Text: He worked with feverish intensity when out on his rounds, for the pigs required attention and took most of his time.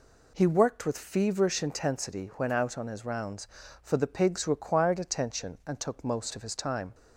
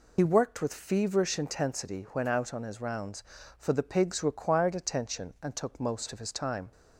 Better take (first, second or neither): first